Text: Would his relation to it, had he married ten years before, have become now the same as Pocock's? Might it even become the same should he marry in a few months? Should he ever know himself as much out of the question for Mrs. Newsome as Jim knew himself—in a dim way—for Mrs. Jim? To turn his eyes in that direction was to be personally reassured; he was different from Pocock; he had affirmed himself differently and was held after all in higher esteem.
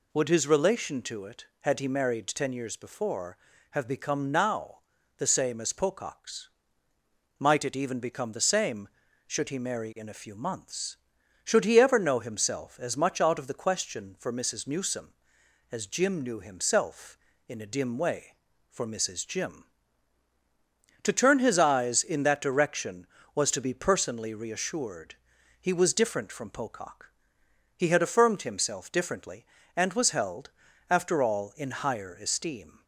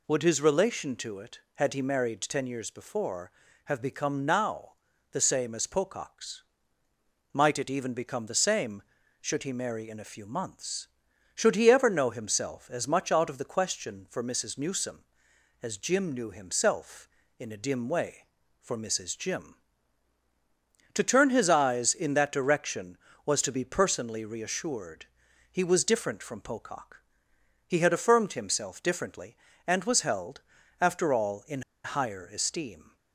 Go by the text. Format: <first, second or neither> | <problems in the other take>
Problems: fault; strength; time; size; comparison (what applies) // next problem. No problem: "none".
first | pauses between "now" and "the"; at 4.7 s; 0.40 s long; also in the first // pauses between "held" and "after"; slight; at 30.4 s; 0.36 s long; slight in the first // pauses between "in" and "higher"; slight; at 31.6 s; 0.22 s long